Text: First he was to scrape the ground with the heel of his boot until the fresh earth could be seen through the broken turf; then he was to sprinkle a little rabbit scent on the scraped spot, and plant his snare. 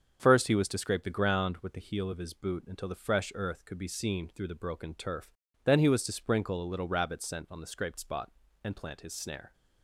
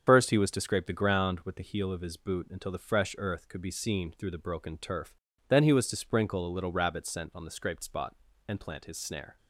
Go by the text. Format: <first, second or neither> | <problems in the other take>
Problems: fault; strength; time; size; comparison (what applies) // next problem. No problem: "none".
first | loses the start of "First"; at 0.0 s; 45 ms // starts louder than the rest; strong; until 1.0 s; 7 dB; also in the first